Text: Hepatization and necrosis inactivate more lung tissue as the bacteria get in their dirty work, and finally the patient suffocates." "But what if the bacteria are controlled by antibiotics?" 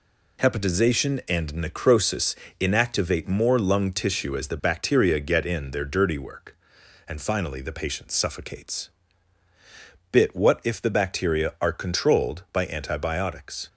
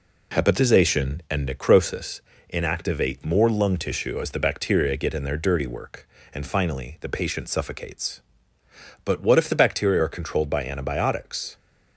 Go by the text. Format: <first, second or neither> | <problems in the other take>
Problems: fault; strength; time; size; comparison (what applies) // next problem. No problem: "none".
second | pauses between "necrosis" and "inactivate"; slight; at 2.3 s; 0.24 s long; slight in the second // says "Bit" for "But"; at 10.1 s